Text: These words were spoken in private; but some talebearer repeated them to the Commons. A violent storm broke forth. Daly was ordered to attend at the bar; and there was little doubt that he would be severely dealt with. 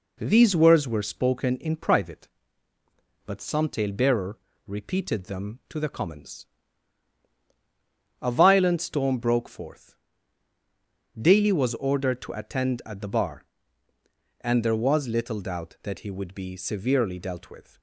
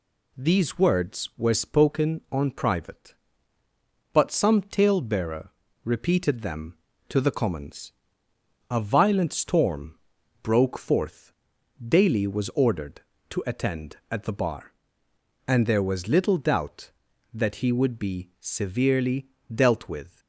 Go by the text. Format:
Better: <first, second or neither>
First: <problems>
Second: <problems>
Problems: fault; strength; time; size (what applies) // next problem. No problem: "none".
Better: first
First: pauses between "talebearer" and "repeated"; slight; at 4.3 s; 0.30 s long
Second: says "on" for "in"; at 2.3 s // pauses between "talebearer" and "repeated"; slight; at 5.5 s; 0.32 s long // pauses between "storm" and "broke"; at 9.9 s; 0.42 s long // pauses between "severely" and "dealt"; slight; at 19.2 s; 0.26 s long